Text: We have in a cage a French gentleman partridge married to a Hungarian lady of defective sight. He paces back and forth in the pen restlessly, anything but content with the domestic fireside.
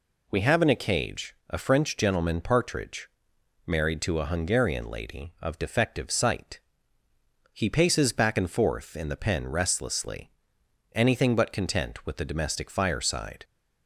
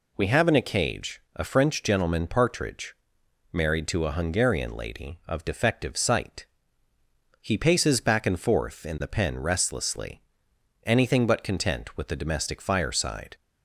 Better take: neither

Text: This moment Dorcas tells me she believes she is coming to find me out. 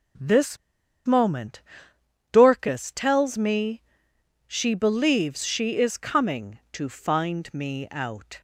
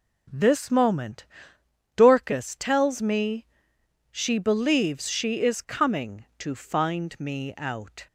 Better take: second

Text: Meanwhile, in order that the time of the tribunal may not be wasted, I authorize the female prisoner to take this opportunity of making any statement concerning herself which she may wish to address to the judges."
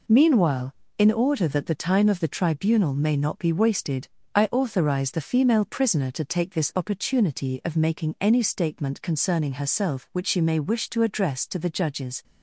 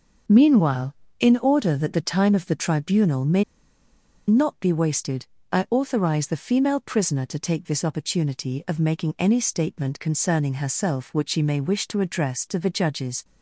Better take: first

